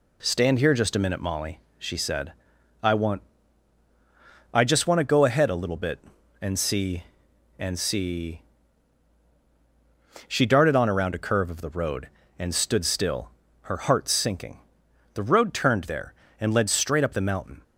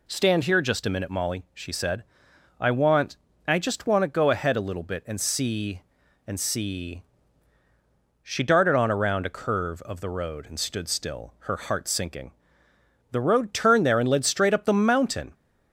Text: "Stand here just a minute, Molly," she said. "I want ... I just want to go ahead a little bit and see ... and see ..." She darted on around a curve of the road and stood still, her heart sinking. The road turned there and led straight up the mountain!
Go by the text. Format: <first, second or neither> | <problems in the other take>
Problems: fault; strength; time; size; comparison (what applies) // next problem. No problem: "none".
neither | none